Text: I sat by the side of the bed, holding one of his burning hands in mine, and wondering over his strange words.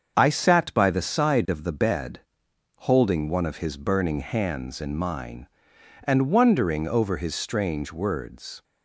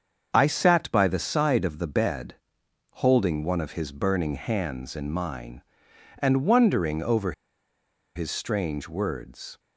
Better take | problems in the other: first | starts louder than the rest; until 1.3 s; 7 dB; also in the first // pauses between "over" and "his"; noticeable; at 7.3 s; 0.83 s long

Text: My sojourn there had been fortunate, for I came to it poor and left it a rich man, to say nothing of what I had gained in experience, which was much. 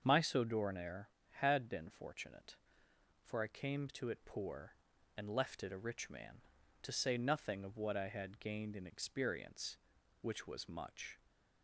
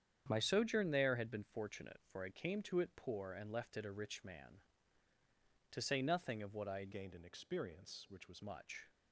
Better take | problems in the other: first | starts louder than the rest; strong; until 1.2 s; 8.5 dB; also in the first // changes voice from "gained" to "was"; from 6.9 to 8.4 s; 1.5 s long

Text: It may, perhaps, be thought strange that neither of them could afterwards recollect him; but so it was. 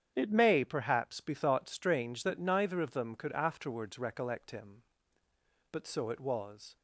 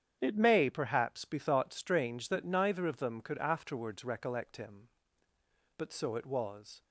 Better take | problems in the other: neither | starts louder than the rest; strong; the same in both

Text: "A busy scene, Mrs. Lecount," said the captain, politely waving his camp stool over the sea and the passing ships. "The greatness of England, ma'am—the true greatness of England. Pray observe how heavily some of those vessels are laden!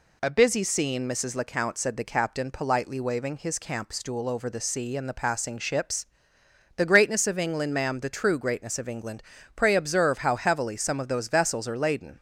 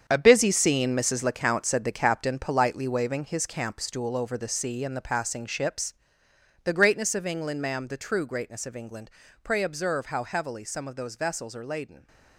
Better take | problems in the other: first | gets quieter; strong; throughout; 10.5 dB

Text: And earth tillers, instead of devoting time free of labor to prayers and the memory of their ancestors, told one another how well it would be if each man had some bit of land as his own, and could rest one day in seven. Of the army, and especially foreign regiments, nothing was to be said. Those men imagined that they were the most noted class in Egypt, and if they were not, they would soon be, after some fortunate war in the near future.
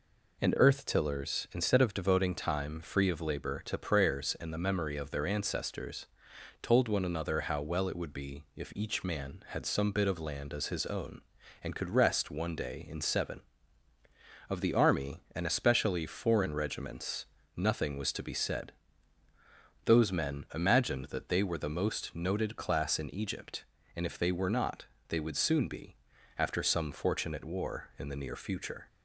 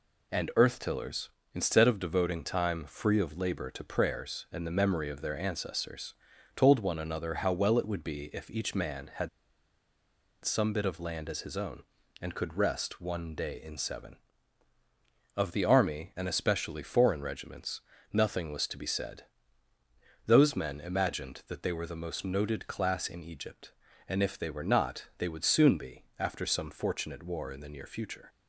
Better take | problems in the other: first | pauses between "had" and "some"; at 9.2 s; 1.1 s long

